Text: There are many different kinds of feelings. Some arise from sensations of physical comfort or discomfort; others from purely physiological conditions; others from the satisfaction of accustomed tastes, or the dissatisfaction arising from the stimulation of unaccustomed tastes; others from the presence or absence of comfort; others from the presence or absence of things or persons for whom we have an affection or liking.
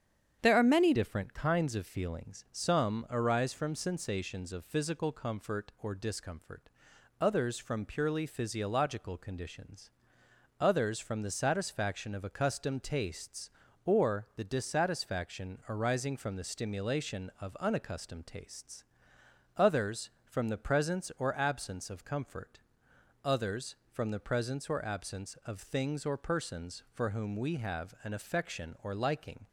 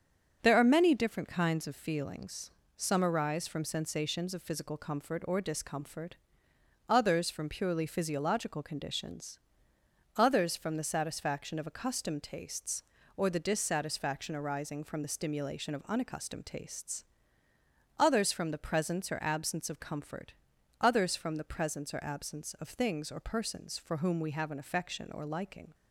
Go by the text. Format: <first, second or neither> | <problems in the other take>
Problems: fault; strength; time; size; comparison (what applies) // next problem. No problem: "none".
second | starts louder than the rest; strong; until 1.4 s; 8.5 dB; also in the second // changes voice at "different"; from 0.9 s on; 28.5 s long